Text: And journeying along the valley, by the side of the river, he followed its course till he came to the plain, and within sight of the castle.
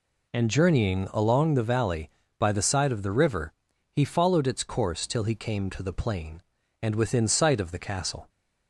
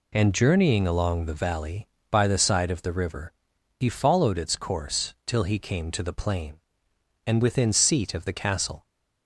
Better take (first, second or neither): first